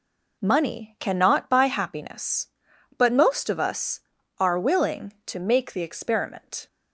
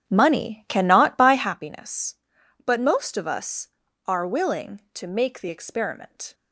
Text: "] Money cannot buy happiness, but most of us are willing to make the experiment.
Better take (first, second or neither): first